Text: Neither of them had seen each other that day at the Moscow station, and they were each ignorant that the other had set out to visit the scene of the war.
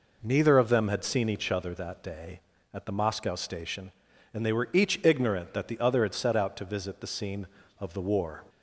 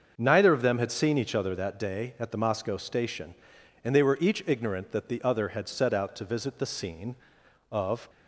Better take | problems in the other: first | starts louder than the rest; until 1.1 s; 6.5 dB // stops before "the war"; at 8.0 s

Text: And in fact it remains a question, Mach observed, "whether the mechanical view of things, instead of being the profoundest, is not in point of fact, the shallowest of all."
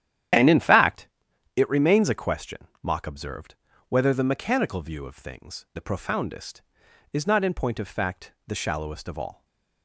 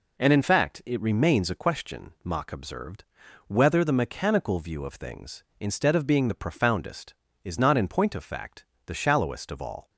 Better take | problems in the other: second | starts louder than the rest; strong; until 1.8 s; 10.5 dB // pauses between "fact" and "it"; noticeable; at 1.0 s; 0.50 s long // skips "instead of being"; at 5.6 s // stays silent after the last word; slight; from 9.3 s on; 0.5 s long

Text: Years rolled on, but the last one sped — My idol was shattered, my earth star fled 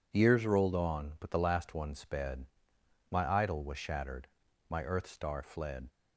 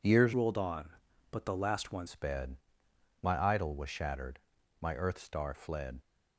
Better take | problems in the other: first | changes voice from "rolled" to "one"; from 0.3 to 2.0 s; 1.7 s long

